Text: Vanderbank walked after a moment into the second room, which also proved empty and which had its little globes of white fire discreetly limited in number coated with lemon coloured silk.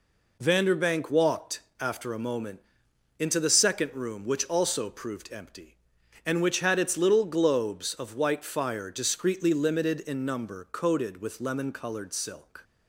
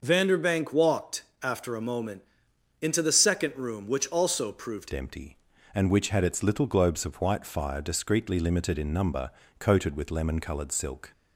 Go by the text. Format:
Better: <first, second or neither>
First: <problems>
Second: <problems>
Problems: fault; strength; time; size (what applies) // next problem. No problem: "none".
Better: first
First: pauses between "walked" and "after"; slight; at 1.5 s; 0.20 s long // pauses between "moment" and "into"; noticeable; at 2.5 s; 0.58 s long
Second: pauses between "walked" and "after"; slight; at 1.2 s; 0.20 s long // pauses between "moment" and "into"; noticeable; at 2.2 s; 0.58 s long // changes voice at "empty"; from 4.9 s on; 6.2 s long // pauses between "number" and "coated"; slight; at 9.2 s; 0.30 s long